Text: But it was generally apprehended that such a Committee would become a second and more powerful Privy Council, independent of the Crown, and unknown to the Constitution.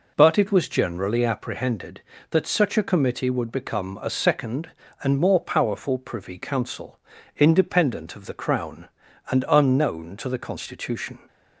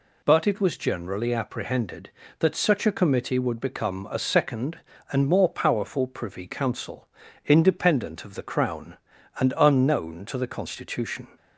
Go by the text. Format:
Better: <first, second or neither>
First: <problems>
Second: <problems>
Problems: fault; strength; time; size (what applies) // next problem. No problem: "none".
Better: second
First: starts louder than the rest; noticeable; until 1.5 s; 4 dB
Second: none